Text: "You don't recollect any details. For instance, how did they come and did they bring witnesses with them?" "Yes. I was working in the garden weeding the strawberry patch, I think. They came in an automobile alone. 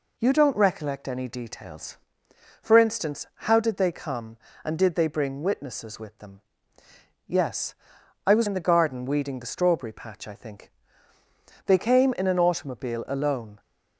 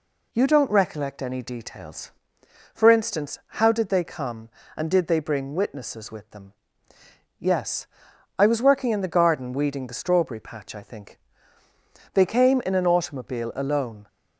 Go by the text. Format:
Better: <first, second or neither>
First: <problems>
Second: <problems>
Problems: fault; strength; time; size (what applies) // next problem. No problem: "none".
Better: second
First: skips "working"; at 8.4 s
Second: none